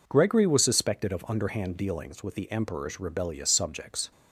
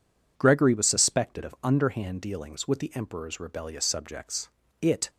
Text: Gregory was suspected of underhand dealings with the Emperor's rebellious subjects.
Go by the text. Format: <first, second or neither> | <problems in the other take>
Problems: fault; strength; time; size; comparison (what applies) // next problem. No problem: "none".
first | goes on to say "It"; slight; from 4.8 s on; 0.28 s long